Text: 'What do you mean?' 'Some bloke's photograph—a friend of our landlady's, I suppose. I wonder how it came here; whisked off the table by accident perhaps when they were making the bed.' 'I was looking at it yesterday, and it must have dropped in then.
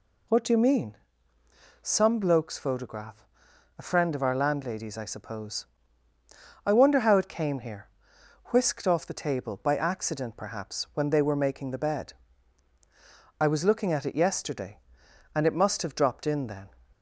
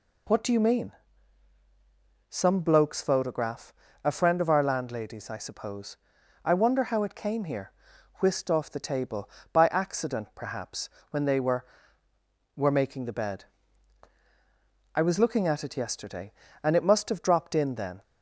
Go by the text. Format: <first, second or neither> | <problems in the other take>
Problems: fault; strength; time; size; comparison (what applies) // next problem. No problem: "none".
first | pauses between "perhaps" and "when"; slight; at 10.8 s; 0.22 s long // says "were" twice; at 12.5 s